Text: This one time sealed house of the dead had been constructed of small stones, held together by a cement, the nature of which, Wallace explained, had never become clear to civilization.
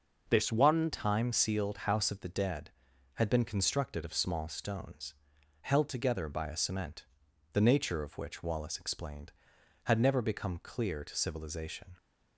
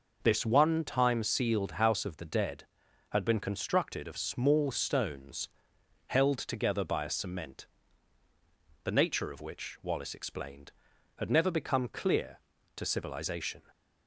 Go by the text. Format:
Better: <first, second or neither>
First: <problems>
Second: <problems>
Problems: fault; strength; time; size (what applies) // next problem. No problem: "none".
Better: second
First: changes voice at "time"; from 0.9 s on; 11.0 s long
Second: none